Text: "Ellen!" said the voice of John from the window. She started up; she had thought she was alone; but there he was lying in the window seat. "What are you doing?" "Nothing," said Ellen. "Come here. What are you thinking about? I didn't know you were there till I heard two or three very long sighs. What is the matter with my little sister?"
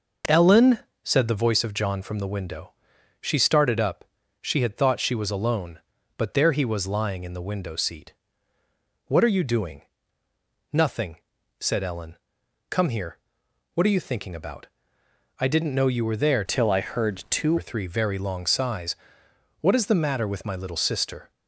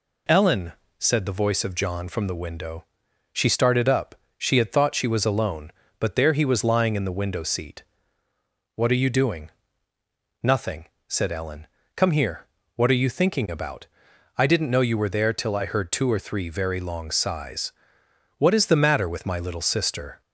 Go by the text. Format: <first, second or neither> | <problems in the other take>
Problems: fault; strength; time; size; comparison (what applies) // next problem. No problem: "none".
second | changes voice from "till" to "two"; from 16.4 to 17.5 s; 1.1 s long